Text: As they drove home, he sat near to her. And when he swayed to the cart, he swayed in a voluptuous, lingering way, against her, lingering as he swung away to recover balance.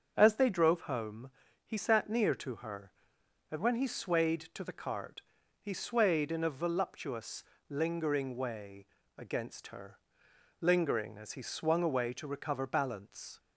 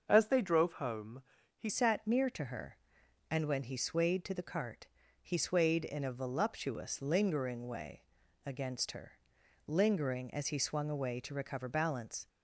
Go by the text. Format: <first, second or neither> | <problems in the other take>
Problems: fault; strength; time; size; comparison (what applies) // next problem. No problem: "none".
first | starts louder than the rest; until 1.1 s; 6.5 dB; also in the first // changes voice at "sat"; from 1.6 s on; 10.6 s long